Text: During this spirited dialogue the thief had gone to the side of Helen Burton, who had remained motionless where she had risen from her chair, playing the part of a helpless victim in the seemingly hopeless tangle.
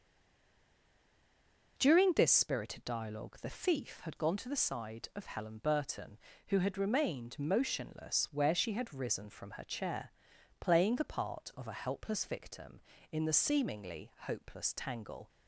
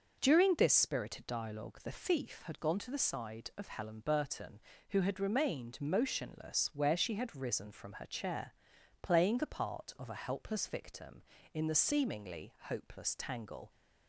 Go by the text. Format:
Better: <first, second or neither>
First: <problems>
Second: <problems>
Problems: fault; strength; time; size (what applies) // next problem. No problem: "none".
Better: second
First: stays silent before the first word; noticeable; until 1.7 s; 1.7 s long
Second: none